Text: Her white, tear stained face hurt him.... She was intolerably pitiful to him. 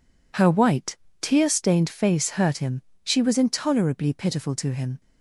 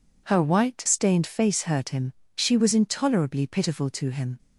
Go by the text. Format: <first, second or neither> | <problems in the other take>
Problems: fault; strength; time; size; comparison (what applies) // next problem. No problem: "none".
first | skips "tear"; at 0.8 s